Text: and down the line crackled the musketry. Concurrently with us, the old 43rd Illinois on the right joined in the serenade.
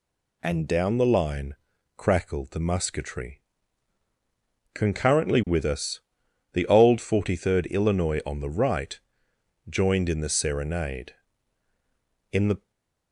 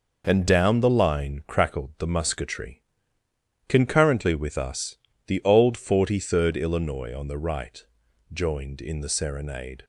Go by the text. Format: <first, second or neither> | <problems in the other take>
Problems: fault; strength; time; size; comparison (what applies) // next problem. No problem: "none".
second | pauses between "line" and "crackled"; at 1.5 s; 0.40 s long // pauses between "right" and "joined"; noticeable; at 8.9 s; 0.70 s long; noticeable in the second // goes on to say "In the"; slight; from 12.3 s on; 0.38 s long // stays silent after the last word; slight; from 12.5 s on; 0.6 s long